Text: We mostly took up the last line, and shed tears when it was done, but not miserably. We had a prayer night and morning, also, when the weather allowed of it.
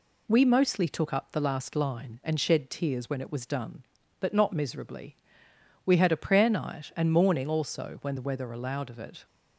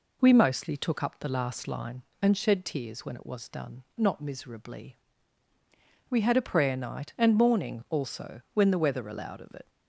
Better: first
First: none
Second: skips "but"; at 3.9 s

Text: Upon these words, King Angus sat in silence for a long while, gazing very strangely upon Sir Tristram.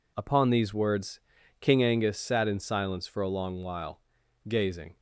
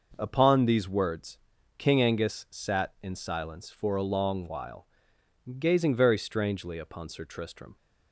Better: second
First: stops before "very strangely upon Sir Tristram"; at 4.9 s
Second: none

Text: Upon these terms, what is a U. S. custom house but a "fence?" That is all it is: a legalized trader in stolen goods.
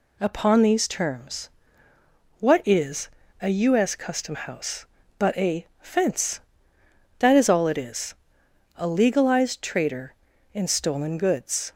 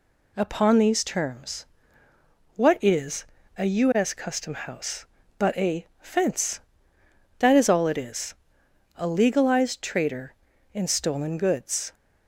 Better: neither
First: pauses between "is" and "a"; slight; at 3.0 s; 0.32 s long // pauses between "a" and "fence"; slight; at 5.6 s; 0.16 s long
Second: pauses between "is" and "a"; slight; at 3.2 s; 0.32 s long // pauses between "a" and "fence"; slight; at 5.8 s; 0.16 s long

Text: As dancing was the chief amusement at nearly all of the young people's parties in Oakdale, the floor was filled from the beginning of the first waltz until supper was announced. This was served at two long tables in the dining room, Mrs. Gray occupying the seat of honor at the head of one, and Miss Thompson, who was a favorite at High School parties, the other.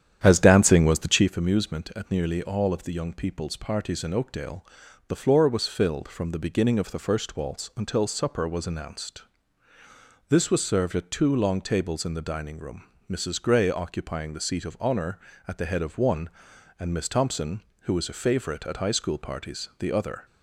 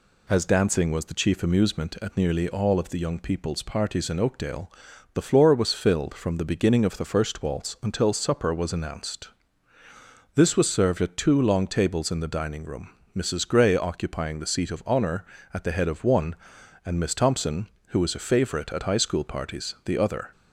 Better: second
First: starts louder than the rest; strong; until 1.3 s; 9.5 dB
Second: none

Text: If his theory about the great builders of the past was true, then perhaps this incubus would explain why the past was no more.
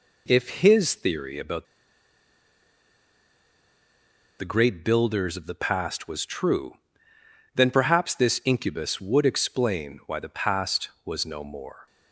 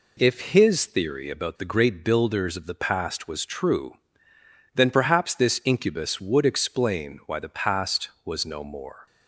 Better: second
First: pauses between "about" and "the"; strong; at 1.6 s; 2.7 s long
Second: none

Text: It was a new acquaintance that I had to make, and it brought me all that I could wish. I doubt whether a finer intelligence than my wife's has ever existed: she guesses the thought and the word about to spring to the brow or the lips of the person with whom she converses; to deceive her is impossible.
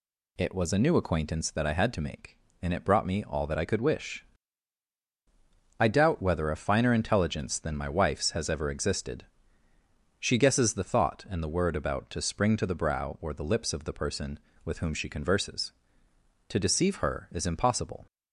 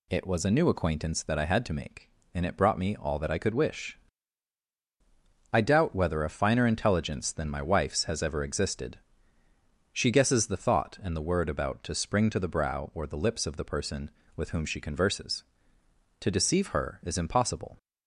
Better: neither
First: none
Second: none

